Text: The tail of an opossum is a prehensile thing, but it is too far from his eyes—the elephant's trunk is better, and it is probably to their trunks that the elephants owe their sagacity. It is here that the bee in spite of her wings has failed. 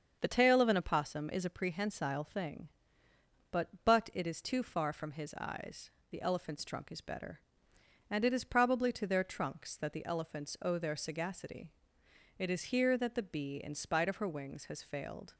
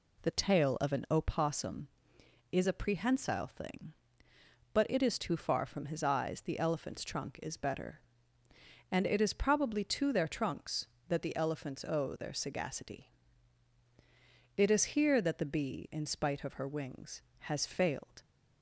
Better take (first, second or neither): second